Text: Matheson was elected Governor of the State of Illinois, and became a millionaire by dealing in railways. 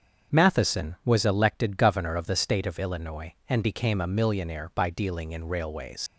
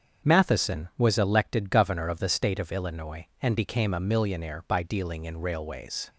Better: second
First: starts louder than the rest; strong; until 1.4 s; 7 dB // leaves "railways" unfinished; at 6.0 s; 115 ms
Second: starts louder than the rest; strong; until 1.3 s; 7.5 dB

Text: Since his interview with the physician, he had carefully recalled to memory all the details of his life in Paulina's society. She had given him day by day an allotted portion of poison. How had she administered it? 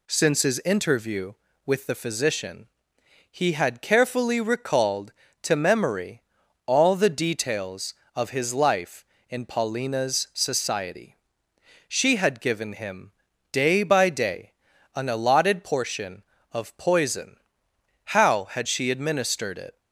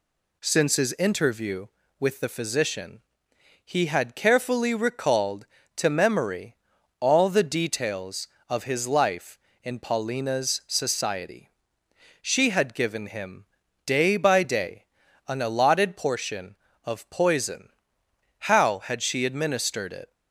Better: neither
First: pauses between "memory" and "all"; at 6.2 s; 0.44 s long // pauses between "him" and "day"; at 13.1 s; 0.40 s long // pauses between "day" and "an"; at 14.5 s; 0.44 s long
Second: pauses between "memory" and "all"; at 6.5 s; 0.44 s long // pauses between "him" and "day"; at 13.4 s; 0.40 s long // pauses between "day" and "an"; at 14.8 s; 0.44 s long

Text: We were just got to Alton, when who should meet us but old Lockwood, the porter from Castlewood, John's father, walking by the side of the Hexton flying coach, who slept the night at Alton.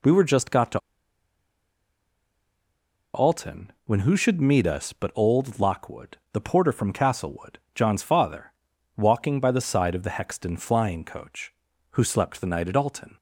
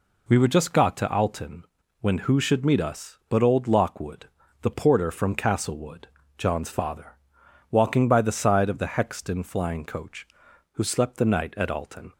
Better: second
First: pauses between "to" and "Alton"; strong; at 0.7 s; 2.3 s long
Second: none

